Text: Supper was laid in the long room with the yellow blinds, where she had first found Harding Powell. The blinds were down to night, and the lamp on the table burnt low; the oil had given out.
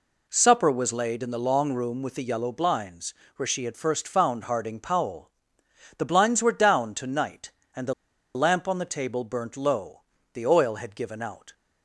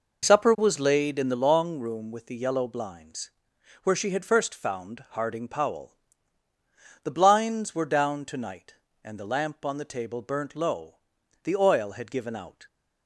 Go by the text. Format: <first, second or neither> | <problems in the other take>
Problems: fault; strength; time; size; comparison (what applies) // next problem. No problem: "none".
second | pauses between "the" and "lamp"; at 7.9 s; 0.41 s long